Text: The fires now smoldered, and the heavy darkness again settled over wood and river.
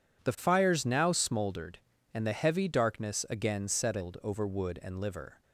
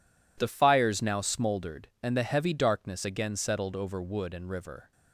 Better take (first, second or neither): second